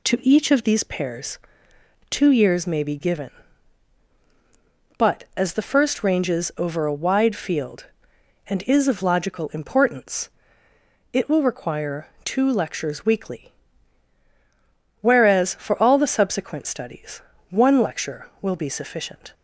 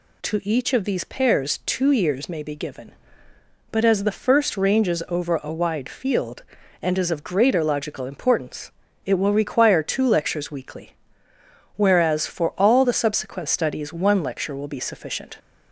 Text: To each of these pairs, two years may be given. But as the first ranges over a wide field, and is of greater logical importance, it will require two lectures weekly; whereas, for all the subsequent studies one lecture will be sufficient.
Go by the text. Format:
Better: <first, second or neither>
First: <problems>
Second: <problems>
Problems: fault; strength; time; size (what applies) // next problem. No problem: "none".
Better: second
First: skips "greater"; at 9.0 s // pauses between "require" and "two"; slight; at 12.0 s; 0.16 s long // pauses between "studies" and "one"; slight; at 17.2 s; 0.28 s long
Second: none